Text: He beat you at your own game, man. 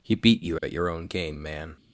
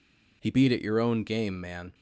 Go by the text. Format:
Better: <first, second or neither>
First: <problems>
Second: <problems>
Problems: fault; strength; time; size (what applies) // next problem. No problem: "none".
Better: first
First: none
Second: skips "you"; at 0.6 s